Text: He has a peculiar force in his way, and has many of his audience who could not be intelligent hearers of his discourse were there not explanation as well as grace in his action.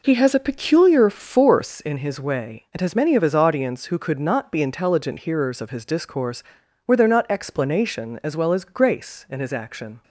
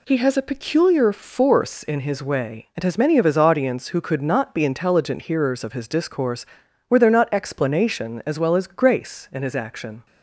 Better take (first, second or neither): second